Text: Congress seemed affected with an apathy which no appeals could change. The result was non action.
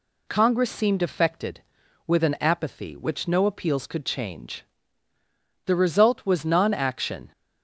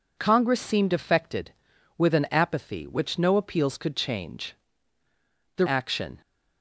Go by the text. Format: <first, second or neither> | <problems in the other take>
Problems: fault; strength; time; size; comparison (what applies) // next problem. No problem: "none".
first | skips "result was non"; at 5.6 s